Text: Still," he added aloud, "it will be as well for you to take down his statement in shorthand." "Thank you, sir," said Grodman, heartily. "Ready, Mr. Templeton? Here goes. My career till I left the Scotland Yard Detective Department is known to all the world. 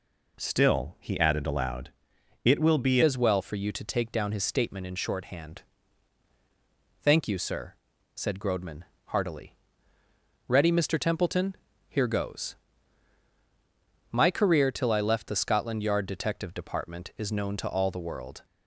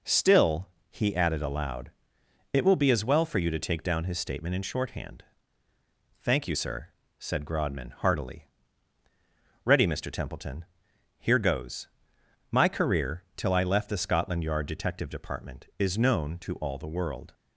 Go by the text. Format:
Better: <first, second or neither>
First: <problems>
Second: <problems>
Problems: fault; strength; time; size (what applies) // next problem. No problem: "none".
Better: second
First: changes voice at "as"; from 3.0 s on; 15.4 s long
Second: none